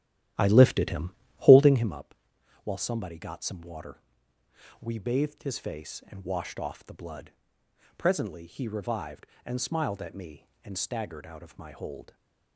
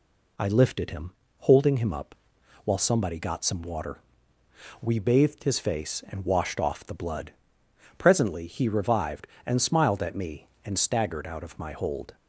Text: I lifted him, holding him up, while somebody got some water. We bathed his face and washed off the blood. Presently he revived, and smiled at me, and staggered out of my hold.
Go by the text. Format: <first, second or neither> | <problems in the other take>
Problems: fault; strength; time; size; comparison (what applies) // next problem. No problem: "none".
second | starts louder than the rest; strong; until 2.0 s; 12 dB